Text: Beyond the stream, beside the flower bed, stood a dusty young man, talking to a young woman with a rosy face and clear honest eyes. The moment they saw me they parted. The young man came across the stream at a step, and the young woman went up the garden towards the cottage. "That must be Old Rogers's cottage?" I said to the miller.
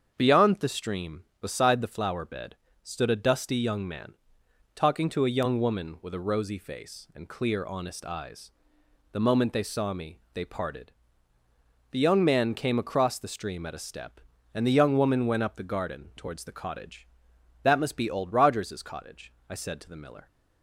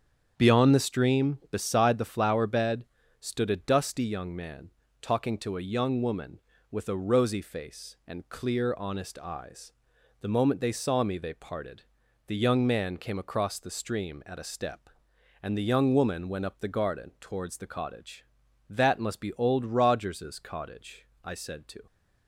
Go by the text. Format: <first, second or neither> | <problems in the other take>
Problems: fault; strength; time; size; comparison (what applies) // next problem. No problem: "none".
first | starts louder than the rest; strong; until 1.3 s; 8 dB; strong in the first // stops before "the miller"; at 21.8 s